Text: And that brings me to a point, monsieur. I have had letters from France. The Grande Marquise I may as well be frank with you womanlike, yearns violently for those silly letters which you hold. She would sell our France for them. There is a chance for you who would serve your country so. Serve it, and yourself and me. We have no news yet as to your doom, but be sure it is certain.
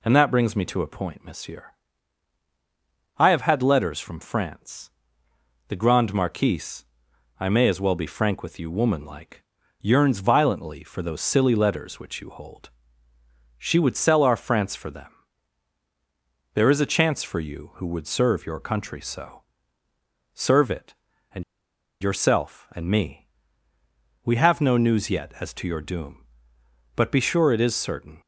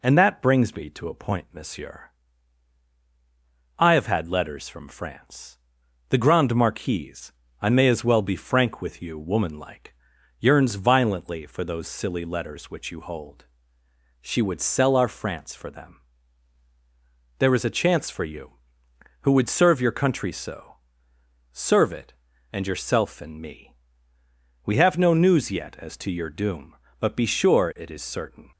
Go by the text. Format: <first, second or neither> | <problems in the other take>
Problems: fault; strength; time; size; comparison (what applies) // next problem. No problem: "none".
second | pauses between "Marquise" and "I"; noticeable; at 6.8 s; 0.54 s long; slight in the second // pauses between "and" and "yourself"; noticeable; at 21.4 s; 0.57 s long